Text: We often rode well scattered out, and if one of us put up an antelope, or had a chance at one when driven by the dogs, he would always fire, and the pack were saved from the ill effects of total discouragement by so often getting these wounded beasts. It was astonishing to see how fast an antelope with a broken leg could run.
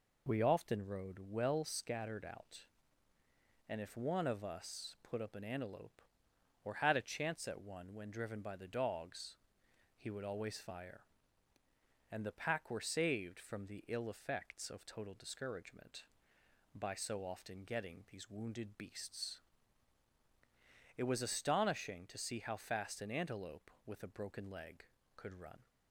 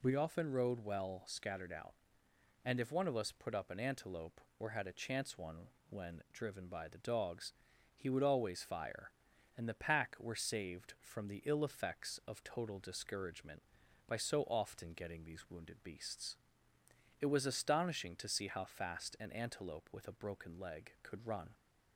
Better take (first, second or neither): first